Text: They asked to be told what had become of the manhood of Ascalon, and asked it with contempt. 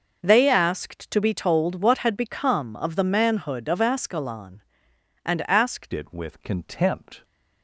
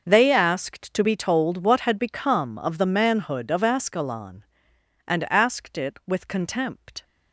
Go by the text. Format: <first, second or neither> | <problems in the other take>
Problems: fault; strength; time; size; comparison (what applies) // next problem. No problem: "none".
second | changes voice at "it"; from 5.9 s on; 1.3 s long